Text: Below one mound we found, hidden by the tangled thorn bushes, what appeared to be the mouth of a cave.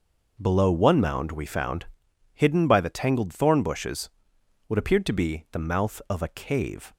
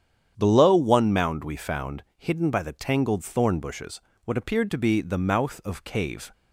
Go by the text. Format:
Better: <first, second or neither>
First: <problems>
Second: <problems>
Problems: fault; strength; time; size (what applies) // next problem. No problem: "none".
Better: first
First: none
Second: starts louder than the rest; strong; until 1.3 s; 9 dB // skips "a"; at 5.8 s